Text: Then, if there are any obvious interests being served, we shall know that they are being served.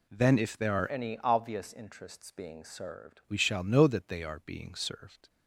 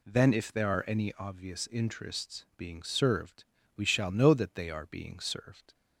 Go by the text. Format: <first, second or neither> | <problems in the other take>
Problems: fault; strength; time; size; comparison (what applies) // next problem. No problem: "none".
second | changes voice from "any" to "served"; from 0.8 to 3.1 s; 2.3 s long